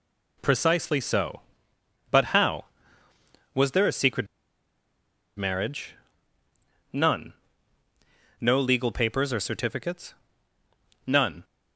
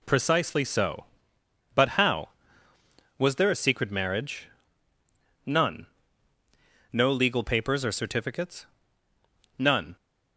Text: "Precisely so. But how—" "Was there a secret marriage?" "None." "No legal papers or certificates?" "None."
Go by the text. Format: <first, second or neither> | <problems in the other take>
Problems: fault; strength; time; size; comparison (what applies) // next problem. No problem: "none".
second | pauses between "secret" and "marriage"; at 4.2 s; 1.1 s long